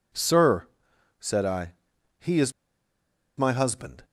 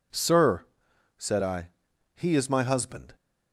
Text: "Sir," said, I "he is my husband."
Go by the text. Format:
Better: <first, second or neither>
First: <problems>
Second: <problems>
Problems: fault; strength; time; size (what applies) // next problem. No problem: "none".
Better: second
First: pauses between "I" and "he"; noticeable; at 1.7 s; 0.46 s long // pauses between "is" and "my"; noticeable; at 2.5 s; 0.85 s long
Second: pauses between "I" and "he"; noticeable; at 1.6 s; 0.46 s long